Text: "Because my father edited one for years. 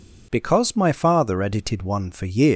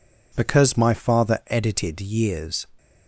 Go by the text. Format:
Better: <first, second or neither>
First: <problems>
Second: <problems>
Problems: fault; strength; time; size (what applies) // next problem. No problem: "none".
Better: first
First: none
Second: skips "one for"; at 1.9 s